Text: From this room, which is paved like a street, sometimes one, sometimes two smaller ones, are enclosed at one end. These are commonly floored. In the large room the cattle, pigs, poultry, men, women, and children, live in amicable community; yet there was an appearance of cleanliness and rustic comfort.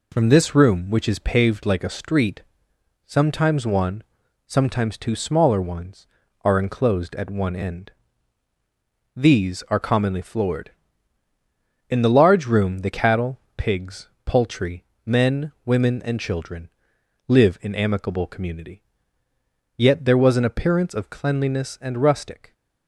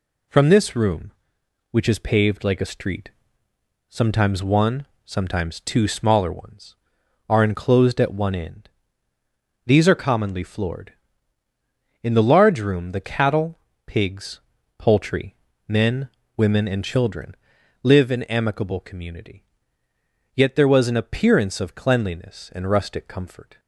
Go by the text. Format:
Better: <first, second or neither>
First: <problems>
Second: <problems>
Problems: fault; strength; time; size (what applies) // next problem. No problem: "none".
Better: second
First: stops before "comfort"; at 22.5 s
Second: none